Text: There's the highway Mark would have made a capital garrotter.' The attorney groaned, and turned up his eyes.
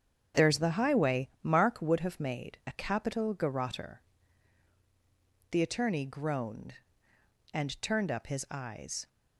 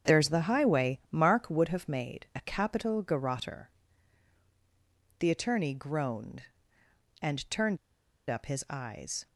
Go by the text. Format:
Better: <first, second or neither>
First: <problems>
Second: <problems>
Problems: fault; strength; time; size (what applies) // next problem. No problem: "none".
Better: first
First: starts louder than the rest; strong; until 1.4 s; 7.5 dB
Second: starts louder than the rest; strong; until 1.1 s; 7.5 dB // pauses between "turned" and "up"; noticeable; at 7.7 s; 0.53 s long